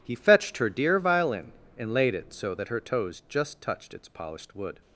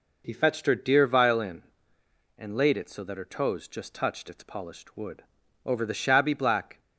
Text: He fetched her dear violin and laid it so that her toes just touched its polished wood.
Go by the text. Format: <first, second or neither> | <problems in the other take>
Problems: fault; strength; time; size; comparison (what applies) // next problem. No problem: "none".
first | goes on to say "Over the shabby black"; noticeable; from 5.6 s on; 1.1 s long